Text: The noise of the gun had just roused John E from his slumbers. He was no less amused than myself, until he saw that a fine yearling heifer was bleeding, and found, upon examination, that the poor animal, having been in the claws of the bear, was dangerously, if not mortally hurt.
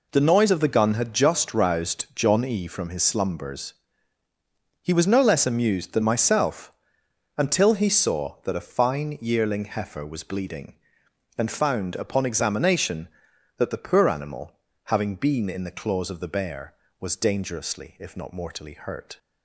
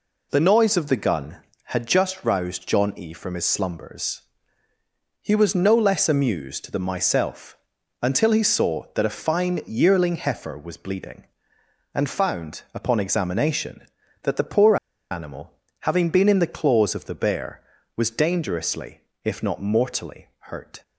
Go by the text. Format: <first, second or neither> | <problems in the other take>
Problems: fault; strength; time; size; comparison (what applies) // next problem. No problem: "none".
first | pauses between "poor" and "animal"; slight; at 14.7 s; 0.35 s long